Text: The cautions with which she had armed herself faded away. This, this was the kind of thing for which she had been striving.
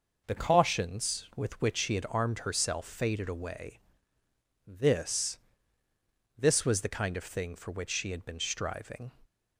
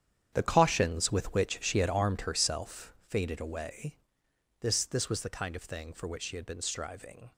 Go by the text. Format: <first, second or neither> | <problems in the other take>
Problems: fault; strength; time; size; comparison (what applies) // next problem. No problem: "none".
first | gets quieter; strong; throughout; 13 dB